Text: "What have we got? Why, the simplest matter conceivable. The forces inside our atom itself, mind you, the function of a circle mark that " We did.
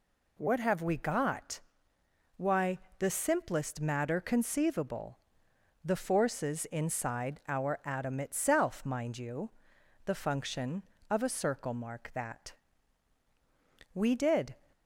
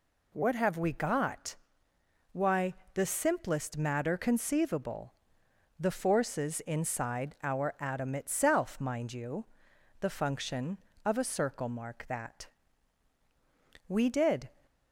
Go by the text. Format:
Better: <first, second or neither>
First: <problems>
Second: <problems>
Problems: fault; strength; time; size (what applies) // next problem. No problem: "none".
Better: neither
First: none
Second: none